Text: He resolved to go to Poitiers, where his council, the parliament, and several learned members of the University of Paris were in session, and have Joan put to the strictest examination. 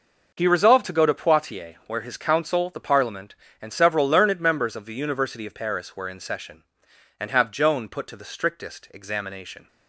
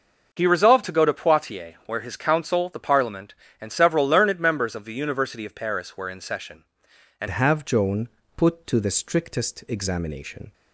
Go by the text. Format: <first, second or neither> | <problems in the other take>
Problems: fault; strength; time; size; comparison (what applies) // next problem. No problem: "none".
first | changes voice at "have"; from 7.2 s on; 3.3 s long // pauses between "Joan" and "put"; slight; at 8.0 s; 0.28 s long